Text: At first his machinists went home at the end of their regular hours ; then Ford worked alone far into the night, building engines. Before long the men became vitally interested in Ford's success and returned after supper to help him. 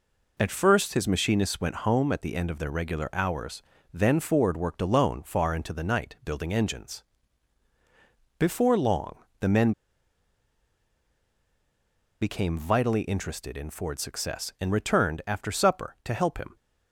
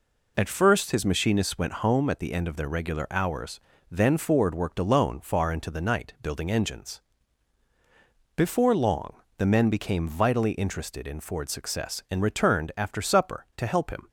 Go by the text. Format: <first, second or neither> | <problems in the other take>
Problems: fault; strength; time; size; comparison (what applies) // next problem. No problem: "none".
second | pauses between "long" and "the"; slight; at 9.1 s; 0.24 s long; slight in the second // pauses between "men" and "became"; strong; at 9.7 s; 2.4 s long